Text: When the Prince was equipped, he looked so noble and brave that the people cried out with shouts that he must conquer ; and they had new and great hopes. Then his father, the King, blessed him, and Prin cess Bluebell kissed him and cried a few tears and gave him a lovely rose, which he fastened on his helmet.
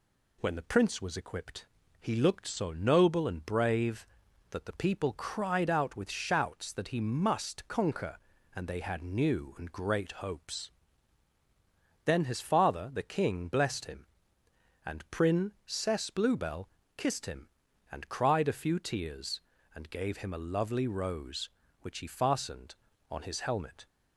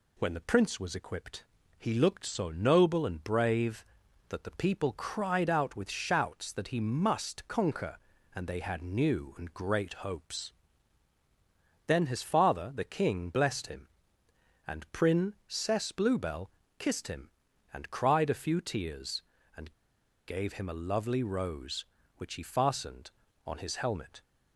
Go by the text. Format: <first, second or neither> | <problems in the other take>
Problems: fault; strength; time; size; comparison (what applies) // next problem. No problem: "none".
first | pauses between "Bluebell" and "kissed"; slight; at 16.4 s; 0.30 s long; slight in the first // pauses between "and" and "gave"; noticeable; at 19.7 s; 0.55 s long